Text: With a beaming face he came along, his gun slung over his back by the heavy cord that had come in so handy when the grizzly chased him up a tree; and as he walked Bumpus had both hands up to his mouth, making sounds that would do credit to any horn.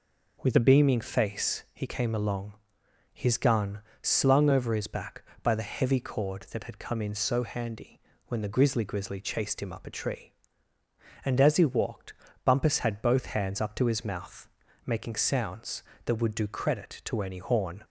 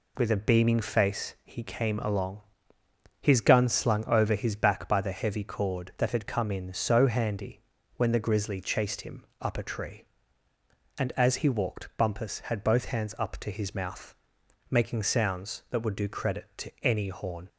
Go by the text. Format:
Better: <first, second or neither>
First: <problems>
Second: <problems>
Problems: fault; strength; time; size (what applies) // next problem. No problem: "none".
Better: second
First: pauses between "gun" and "slung"; slight; at 3.8 s; 0.22 s long // pauses between "handy" and "when"; slight; at 8.0 s; 0.24 s long // says "grizzly" twice; at 8.8 s // pauses between "walked" and "Bumpus"; slight; at 12.1 s; 0.32 s long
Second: pauses between "handy" and "when"; slight; at 7.6 s; 0.34 s long